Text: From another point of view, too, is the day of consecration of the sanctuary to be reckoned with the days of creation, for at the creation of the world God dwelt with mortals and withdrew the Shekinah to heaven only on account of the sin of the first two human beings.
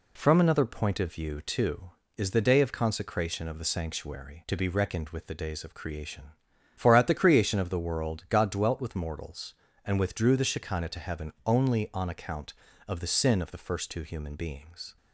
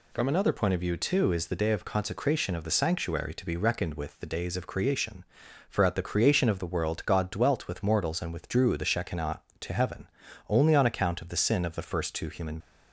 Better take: first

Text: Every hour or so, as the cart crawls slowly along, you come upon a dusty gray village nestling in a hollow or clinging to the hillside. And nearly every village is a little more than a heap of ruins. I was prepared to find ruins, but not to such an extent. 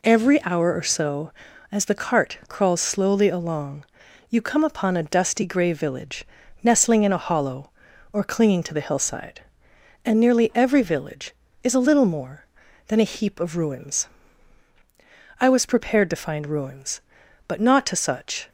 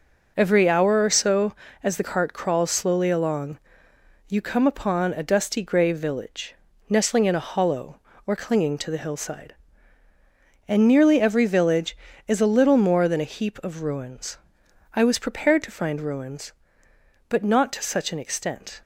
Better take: second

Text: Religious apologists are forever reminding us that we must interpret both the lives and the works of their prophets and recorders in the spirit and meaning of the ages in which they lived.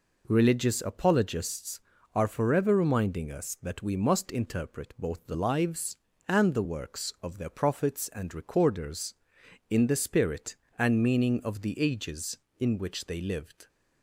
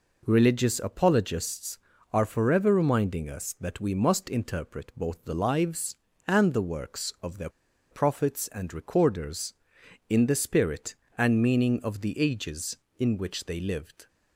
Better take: first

